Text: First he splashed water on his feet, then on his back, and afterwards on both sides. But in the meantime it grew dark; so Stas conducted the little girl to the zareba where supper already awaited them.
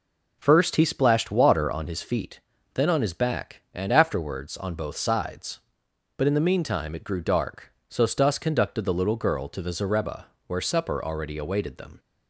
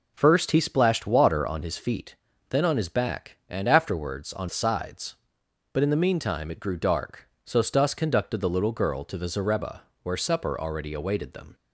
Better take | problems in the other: first | skips "both"; at 4.4 s // pauses between "zareba" and "where"; slight; at 9.8 s; 0.20 s long; slight in the first

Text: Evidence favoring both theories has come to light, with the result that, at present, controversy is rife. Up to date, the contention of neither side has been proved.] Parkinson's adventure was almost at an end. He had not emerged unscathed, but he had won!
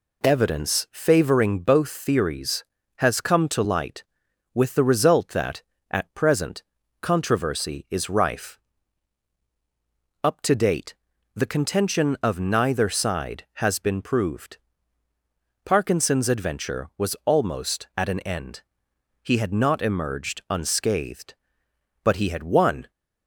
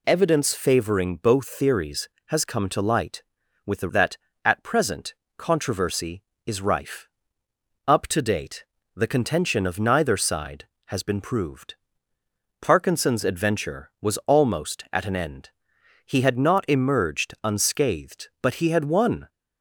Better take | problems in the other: first | skips "result"; at 3.8 s

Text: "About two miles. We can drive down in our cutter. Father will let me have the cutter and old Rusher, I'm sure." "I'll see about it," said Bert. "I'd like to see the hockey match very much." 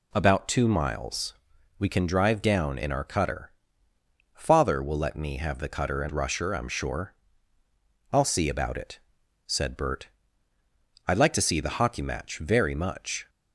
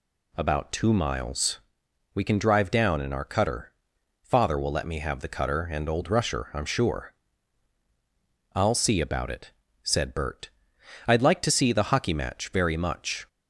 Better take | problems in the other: second | skips "old"; at 6.1 s

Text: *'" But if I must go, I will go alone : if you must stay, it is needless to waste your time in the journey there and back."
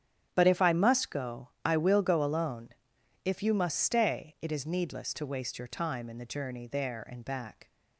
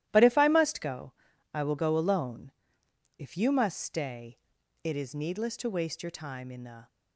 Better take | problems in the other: first | starts louder than the rest; strong; until 1.1 s; 13.5 dB; strong in the first // stops before "journey there and back"; at 6.8 s

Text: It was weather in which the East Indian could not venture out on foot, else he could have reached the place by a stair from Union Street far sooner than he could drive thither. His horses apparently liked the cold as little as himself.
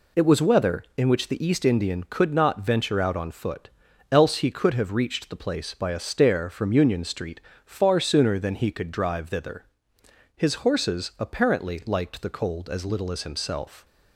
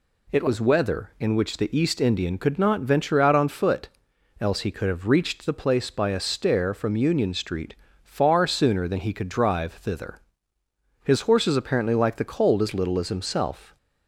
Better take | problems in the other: neither | pauses between "Street" and "far"; slight; the same in both

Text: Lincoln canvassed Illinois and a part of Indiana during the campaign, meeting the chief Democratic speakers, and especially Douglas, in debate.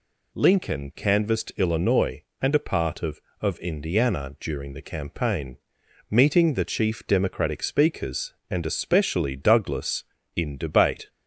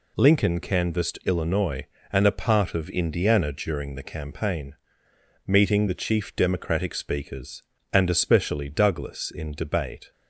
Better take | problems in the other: second | says "of" twice; at 3.4 s

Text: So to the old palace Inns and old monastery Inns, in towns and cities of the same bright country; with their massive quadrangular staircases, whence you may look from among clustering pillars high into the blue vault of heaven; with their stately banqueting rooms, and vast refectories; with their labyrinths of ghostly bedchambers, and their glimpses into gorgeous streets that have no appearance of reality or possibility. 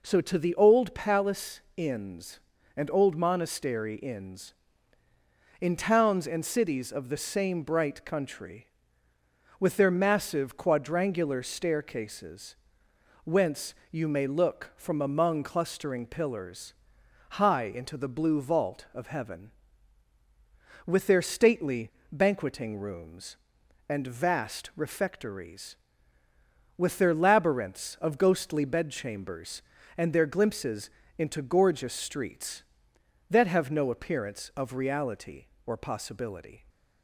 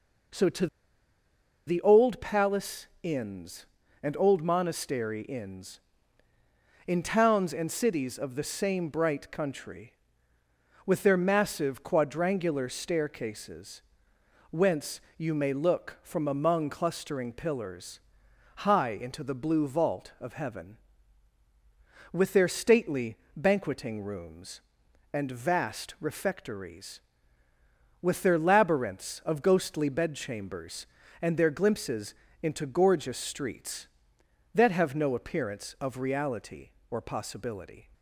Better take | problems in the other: first | pauses between "to" and "the"; at 0.6 s; 1.0 s long // pauses between "palace" and "Inns"; slight; at 2.8 s; 0.16 s long; slight in the first // pauses between "whence" and "you"; slight; at 15.0 s; 0.16 s long; slight in the first // pauses between "pillars" and "high"; noticeable; at 17.9 s; 0.56 s long; noticeable in the first // pauses between "stately" and "banqueting"; slight; at 23.1 s; 0.20 s long; slight in the first // pauses between "glimpses" and "into"; slight; at 32.1 s; 0.26 s long; slight in the first

